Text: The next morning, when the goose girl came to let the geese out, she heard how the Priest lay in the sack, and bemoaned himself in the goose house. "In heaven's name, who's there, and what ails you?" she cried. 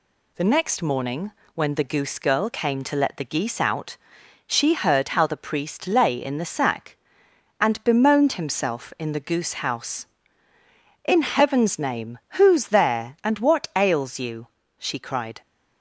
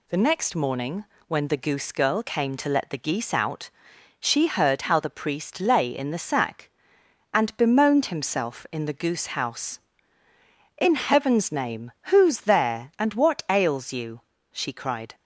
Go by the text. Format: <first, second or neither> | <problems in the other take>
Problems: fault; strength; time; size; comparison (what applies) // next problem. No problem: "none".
neither | none